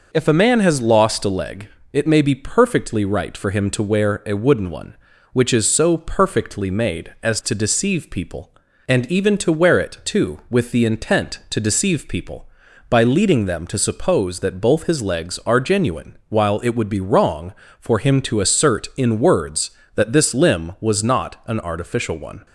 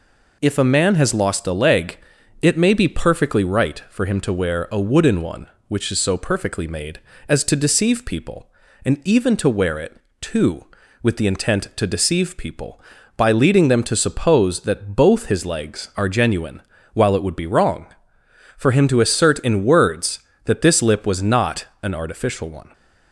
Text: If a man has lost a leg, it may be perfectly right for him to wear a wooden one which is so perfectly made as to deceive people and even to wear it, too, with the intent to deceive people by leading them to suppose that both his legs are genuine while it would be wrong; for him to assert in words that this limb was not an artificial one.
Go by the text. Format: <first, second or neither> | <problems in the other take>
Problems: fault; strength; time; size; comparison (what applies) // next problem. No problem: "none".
first | pauses between "genuine" and "while"; slight; at 16.6 s; 0.32 s long // says "lip" for "limb"; at 20.8 s // pauses between "not" and "an"; slight; at 21.6 s; 0.16 s long